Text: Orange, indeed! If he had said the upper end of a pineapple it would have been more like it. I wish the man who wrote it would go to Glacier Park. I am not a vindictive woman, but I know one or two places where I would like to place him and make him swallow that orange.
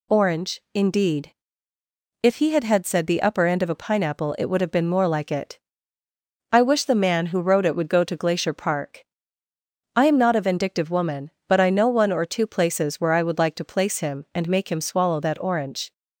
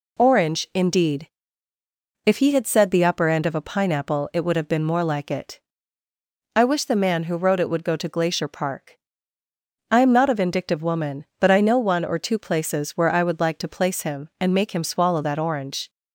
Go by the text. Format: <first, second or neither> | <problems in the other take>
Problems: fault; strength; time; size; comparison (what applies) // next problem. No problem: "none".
second | says "had" twice; at 2.6 s